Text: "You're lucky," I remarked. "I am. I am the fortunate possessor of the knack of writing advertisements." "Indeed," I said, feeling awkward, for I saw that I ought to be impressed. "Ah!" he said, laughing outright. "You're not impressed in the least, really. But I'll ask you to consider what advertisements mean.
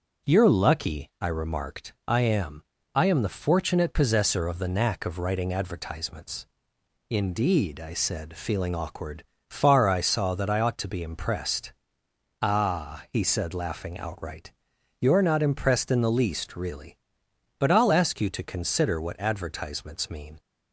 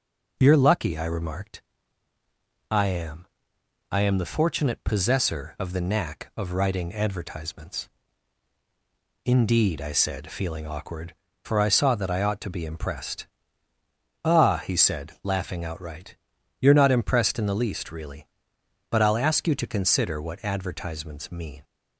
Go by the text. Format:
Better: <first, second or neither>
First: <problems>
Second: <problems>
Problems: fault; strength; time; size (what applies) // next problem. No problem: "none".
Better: second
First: says "far" for "for"; at 9.4 s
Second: none